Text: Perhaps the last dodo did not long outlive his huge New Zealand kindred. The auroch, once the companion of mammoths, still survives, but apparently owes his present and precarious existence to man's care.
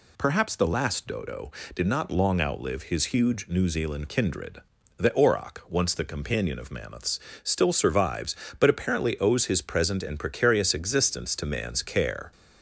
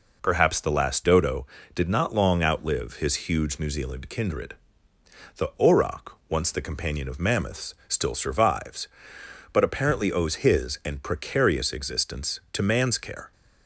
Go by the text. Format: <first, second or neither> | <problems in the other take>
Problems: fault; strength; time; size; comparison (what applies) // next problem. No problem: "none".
first | skips "present"; at 10.8 s